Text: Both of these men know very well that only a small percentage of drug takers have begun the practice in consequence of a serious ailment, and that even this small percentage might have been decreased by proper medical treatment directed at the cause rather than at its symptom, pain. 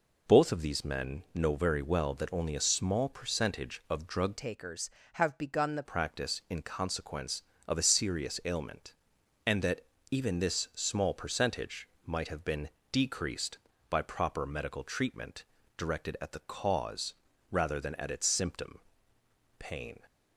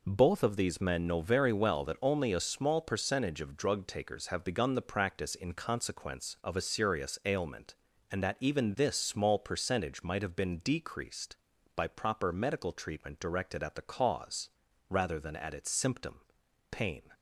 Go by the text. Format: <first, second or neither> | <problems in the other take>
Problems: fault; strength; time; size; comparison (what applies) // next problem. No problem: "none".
second | changes voice from "takers" to "the"; from 4.3 to 5.8 s; 1.5 s long // pauses between "that" and "even"; slight; at 9.8 s; 0.28 s long // pauses between "percentage" and "might"; slight; at 11.8 s; 0.16 s long // pauses between "been" and "decreased"; slight; at 12.7 s; 0.20 s long // pauses between "treatment" and "directed"; slight; at 15.4 s; 0.32 s long // pauses between "cause" and "rather"; slight; at 17.1 s; 0.36 s long; also in the second